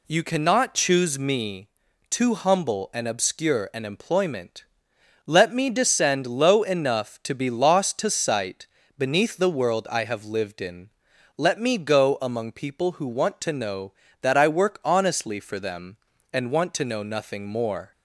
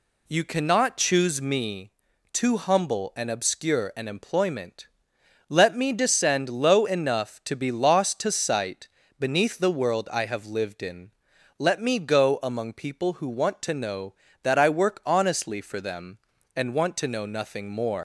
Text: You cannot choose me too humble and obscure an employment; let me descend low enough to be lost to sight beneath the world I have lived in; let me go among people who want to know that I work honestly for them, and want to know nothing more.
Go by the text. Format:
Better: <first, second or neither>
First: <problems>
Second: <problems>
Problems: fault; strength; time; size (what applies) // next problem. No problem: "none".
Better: first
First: pauses between "me" and "too"; at 1.6 s; 0.40 s long // pauses between "sight" and "beneath"; slight; at 8.6 s; 0.32 s long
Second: pauses between "me" and "too"; at 1.9 s; 0.40 s long // pauses between "sight" and "beneath"; slight; at 8.8 s; 0.32 s long // leaves "more" unfinished; at 17.9 s; 110 ms